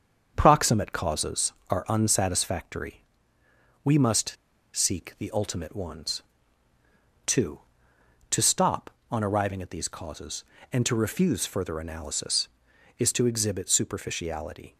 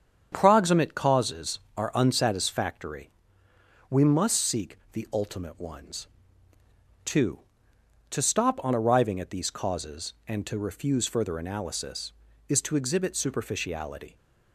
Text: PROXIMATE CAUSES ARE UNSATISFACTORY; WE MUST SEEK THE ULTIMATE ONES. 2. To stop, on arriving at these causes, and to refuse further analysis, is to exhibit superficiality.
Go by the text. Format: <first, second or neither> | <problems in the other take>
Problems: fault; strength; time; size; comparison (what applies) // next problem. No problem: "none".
second | starts louder than the rest; strong; until 1.3 s; 7 dB; strong in the second // pauses between "MUST" and "SEEK"; at 4.3 s; 0.39 s long